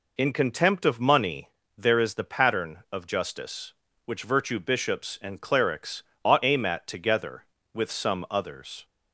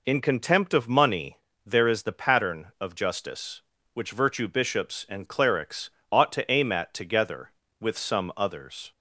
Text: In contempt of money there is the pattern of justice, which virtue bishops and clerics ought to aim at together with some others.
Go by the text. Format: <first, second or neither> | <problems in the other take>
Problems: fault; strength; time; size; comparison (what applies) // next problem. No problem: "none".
second | pauses between "money" and "there"; slight; at 1.5 s; 0.26 s long; slight in the second // pauses between "clerics" and "ought"; slight; at 6.0 s; 0.22 s long; slight in the second // skips "to"; at 6.4 s